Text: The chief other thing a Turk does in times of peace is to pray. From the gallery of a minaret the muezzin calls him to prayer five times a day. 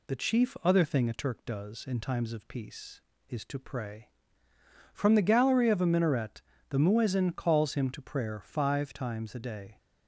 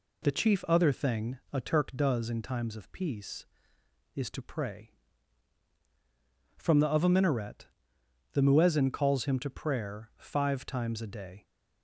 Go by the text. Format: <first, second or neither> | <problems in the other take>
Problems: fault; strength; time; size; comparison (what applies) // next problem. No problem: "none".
first | skips "gallery"; at 6.8 s // pauses between "minaret" and "the"; noticeable; at 7.6 s; 0.66 s long; slight in the first